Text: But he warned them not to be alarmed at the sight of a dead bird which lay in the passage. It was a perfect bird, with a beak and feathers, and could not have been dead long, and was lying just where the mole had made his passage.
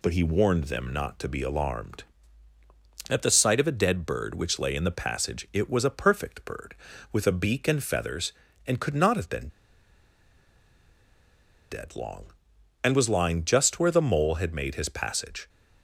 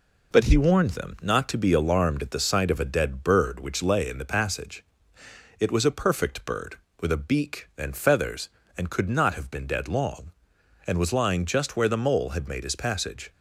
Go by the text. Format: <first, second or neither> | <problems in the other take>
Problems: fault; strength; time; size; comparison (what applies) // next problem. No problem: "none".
second | pauses between "been" and "dead"; strong; at 9.4 s; 2.2 s long